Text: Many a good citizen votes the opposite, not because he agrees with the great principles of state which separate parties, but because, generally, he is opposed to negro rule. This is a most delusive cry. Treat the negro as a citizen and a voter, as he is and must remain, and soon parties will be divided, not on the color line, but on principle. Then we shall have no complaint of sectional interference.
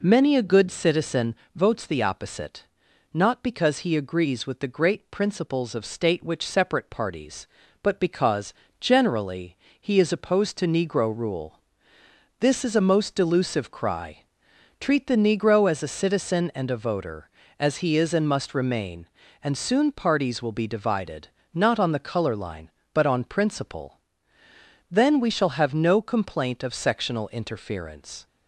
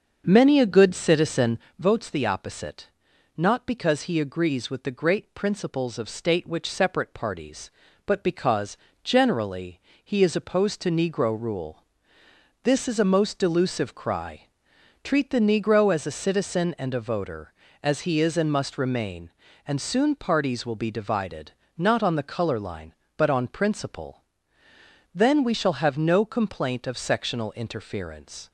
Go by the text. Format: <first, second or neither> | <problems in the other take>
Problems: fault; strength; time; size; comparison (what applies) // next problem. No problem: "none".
first | starts louder than the rest; until 1.9 s; 6.5 dB // pauses between "citizen" and "votes"; slight; at 1.5 s; 0.18 s long; slight in the first